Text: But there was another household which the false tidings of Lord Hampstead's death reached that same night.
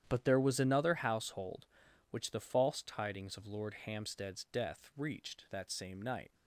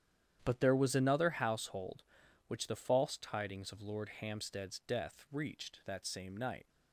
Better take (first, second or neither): neither